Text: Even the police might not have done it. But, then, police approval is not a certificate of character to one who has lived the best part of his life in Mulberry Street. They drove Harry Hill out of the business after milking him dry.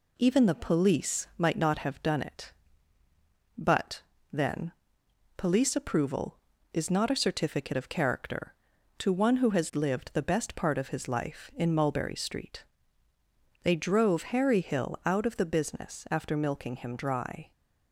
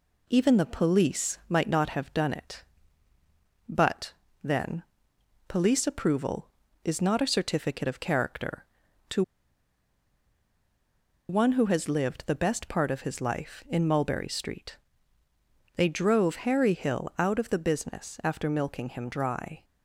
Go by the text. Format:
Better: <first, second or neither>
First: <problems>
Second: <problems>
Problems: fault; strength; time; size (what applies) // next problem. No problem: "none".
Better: first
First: none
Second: pauses between "to" and "one"; strong; at 9.2 s; 2.0 s long